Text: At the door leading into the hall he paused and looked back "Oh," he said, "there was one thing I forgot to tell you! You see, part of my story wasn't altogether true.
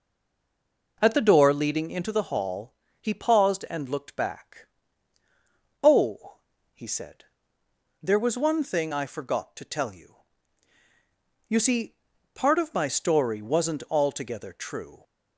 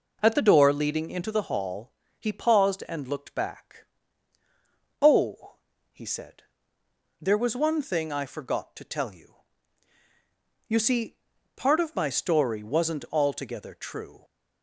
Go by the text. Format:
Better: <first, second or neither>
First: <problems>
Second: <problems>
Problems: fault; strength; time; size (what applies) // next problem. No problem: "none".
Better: second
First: stays silent before the first word; until 0.9 s; 0.9 s long // pauses between "hall" and "he"; slight; at 2.7 s; 0.28 s long // pauses between "back" and "Oh"; at 4.6 s; 1.1 s long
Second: pauses between "hall" and "he"; slight; at 1.9 s; 0.28 s long // pauses between "back" and "Oh"; at 3.8 s; 1.1 s long